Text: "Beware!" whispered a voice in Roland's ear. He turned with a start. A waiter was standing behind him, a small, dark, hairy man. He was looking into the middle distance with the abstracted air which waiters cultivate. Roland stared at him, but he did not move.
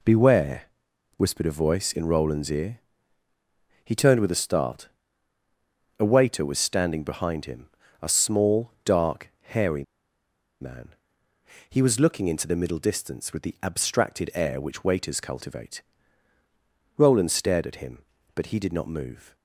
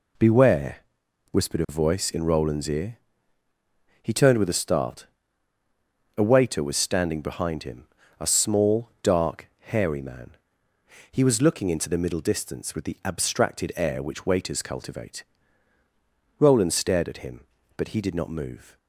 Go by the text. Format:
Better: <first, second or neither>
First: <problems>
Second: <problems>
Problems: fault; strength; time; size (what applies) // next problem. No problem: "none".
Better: second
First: pauses between "hairy" and "man"; noticeable; at 9.8 s; 0.78 s long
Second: none